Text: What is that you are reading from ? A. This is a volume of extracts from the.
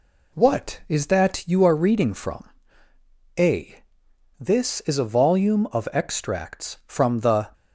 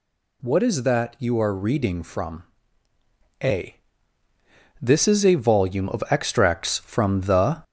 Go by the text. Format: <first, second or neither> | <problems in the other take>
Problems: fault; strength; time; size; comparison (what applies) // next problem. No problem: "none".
first | gets louder; slight; throughout; 3 dB